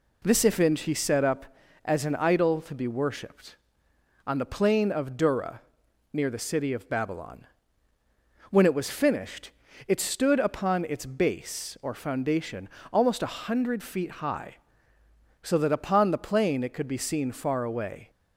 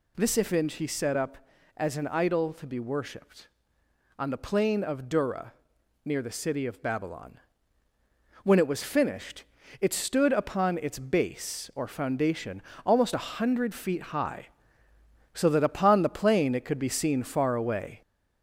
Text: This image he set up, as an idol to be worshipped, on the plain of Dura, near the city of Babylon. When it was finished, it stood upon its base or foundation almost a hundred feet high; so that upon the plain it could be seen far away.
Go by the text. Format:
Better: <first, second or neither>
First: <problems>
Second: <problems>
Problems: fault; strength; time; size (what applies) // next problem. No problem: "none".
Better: first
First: pauses between "foundation" and "almost"; slight; at 12.6 s; 0.24 s long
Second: gets louder; throughout; 3.5 dB // pauses between "foundation" and "almost"; slight; at 12.6 s; 0.24 s long